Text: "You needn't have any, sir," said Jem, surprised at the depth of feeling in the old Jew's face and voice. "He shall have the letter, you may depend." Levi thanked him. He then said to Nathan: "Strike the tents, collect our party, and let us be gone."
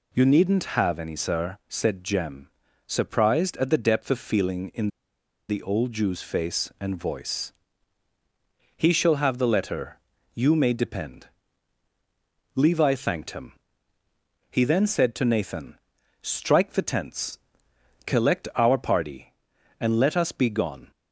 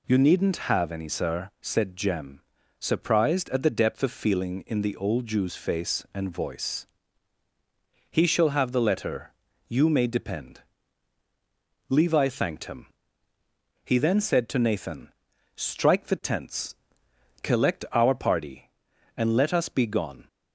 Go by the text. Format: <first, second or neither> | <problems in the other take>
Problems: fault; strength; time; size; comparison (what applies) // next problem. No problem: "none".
second | pauses between "in" and "the"; noticeable; at 4.8 s; 0.61 s long